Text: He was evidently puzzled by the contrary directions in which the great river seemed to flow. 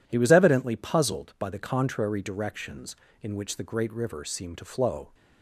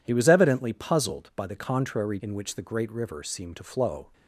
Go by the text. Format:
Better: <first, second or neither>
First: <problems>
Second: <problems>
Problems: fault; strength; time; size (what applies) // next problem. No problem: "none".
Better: first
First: none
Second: skips "directions"; at 2.1 s